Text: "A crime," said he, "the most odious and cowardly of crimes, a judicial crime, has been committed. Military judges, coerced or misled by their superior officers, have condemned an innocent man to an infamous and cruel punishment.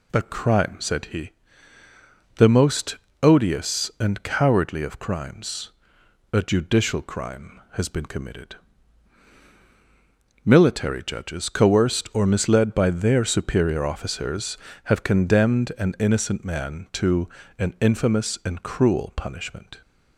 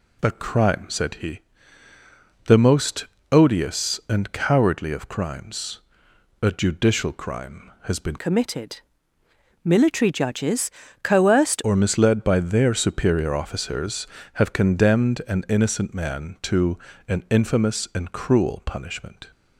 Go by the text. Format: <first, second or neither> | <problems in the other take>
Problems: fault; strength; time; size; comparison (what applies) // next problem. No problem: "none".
first | pauses between "most" and "odious"; slight; at 3.0 s; 0.26 s long; slight in the first // changes voice from "committed" to "coerced"; from 8.1 to 11.6 s; 3.5 s long // pauses between "to" and "an"; slight; at 16.7 s; 0.32 s long; slight in the first